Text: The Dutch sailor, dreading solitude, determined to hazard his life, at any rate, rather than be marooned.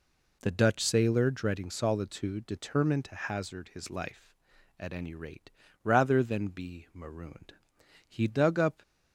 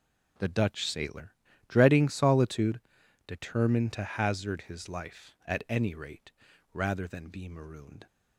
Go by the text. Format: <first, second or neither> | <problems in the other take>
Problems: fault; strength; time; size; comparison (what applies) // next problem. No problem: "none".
second | goes on to say "He dug up"; noticeable; from 8.0 s on; 0.74 s long